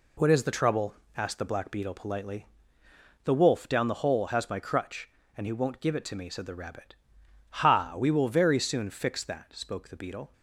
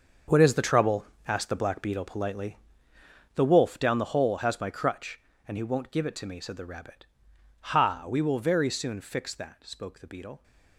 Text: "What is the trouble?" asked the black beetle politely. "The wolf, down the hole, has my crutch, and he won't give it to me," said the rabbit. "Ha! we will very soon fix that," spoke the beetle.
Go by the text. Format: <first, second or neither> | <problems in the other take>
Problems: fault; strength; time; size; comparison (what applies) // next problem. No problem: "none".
first | gets quieter; strong; throughout; 12.5 dB